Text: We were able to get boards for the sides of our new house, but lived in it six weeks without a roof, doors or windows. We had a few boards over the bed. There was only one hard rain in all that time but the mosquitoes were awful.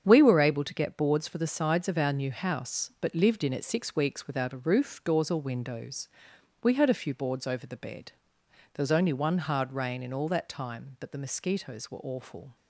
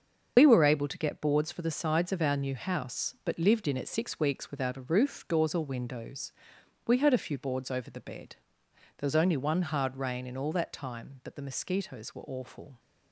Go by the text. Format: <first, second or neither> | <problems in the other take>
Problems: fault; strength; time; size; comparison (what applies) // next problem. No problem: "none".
first | loses the start of "We"; at 0.3 s; 80 ms // starts louder than the rest; until 1.3 s; 6.5 dB; strong in the first